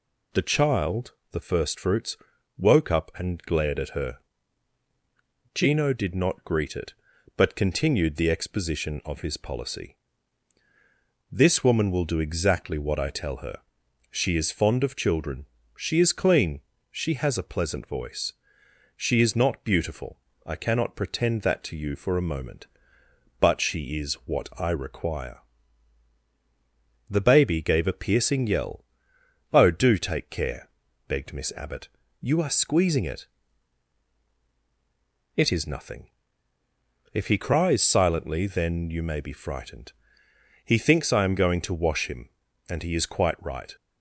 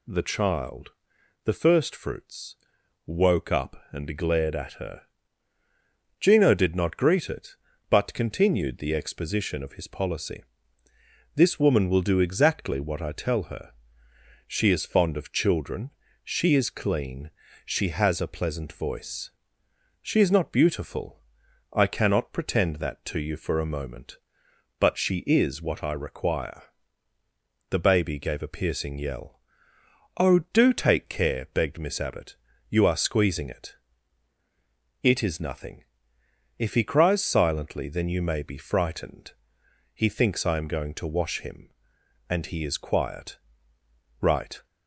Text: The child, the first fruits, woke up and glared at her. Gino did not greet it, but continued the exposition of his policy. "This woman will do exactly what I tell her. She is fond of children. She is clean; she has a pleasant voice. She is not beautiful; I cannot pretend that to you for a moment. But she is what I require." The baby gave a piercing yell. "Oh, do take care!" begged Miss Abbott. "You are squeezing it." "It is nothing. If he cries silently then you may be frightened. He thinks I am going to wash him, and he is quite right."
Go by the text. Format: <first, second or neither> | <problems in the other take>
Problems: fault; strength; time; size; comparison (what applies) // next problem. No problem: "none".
first | says "quiet" for "quite"; at 42.7 s